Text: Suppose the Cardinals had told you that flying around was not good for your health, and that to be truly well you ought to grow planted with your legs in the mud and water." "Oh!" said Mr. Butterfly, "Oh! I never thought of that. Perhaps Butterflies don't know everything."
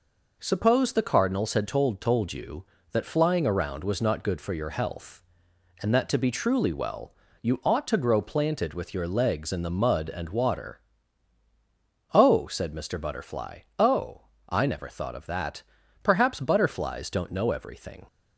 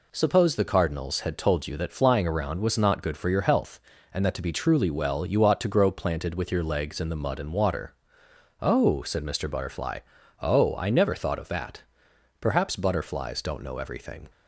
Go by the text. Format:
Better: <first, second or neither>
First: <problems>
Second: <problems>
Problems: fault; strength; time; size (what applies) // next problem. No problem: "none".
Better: second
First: says "told" twice; at 1.9 s // pauses between "well" and "you"; slight; at 7.1 s; 0.28 s long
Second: none